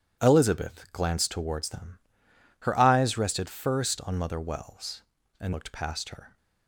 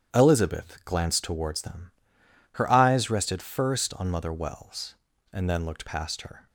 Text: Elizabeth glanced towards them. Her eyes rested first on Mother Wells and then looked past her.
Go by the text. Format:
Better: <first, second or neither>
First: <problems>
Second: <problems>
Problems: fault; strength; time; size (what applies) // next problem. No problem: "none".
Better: second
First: starts louder than the rest; strong; until 1.2 s; 10 dB // skips "then"; at 5.5 s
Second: starts louder than the rest; strong; until 1.2 s; 9.5 dB